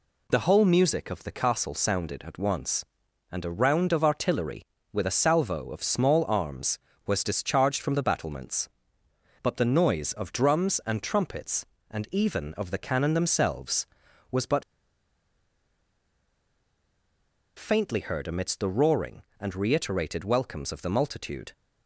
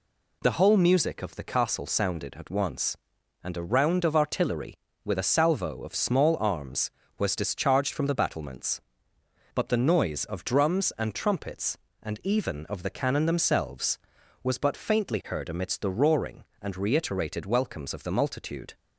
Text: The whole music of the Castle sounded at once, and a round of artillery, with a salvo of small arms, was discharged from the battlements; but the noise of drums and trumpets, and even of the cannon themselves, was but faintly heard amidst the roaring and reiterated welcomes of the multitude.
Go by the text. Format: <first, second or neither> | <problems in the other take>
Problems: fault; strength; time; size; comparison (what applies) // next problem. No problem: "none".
second | pauses between "but" and "faintly"; strong; at 14.6 s; 2.9 s long